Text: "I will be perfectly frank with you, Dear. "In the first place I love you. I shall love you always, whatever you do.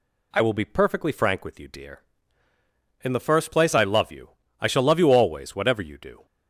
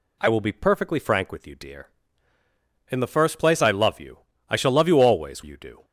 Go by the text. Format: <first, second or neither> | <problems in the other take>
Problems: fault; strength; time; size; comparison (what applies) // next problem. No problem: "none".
first | skips "whatever"; at 5.4 s